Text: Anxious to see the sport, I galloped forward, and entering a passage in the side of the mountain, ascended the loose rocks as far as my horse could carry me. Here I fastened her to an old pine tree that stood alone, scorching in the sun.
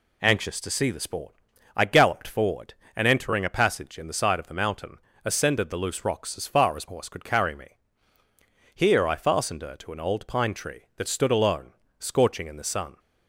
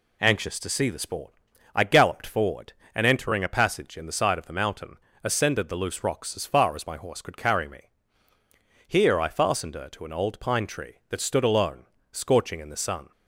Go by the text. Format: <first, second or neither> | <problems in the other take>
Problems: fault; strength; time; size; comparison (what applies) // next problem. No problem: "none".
second | skips "my"; at 6.8 s